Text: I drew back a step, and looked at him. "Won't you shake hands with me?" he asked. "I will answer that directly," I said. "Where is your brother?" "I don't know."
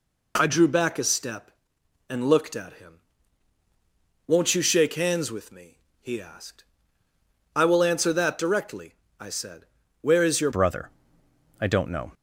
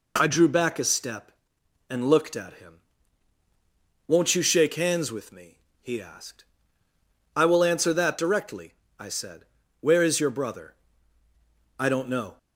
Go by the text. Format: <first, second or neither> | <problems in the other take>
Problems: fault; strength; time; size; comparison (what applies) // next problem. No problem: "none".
second | changes voice at "brother"; from 10.5 s on; 1.6 s long